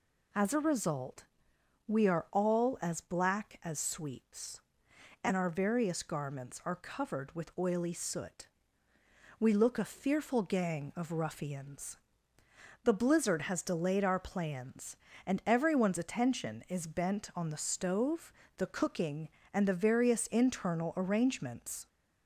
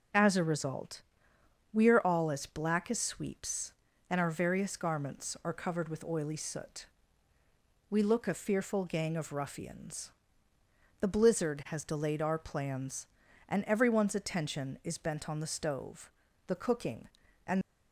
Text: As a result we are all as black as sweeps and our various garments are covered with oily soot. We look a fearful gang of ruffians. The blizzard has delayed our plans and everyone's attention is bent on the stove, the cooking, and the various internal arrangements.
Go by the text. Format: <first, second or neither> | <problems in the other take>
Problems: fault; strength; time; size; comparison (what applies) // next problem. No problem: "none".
first | pauses between "result" and "we"; noticeable; at 1.0 s; 0.70 s long; noticeable in the first // stops before "the various internal arrangements"; at 17.6 s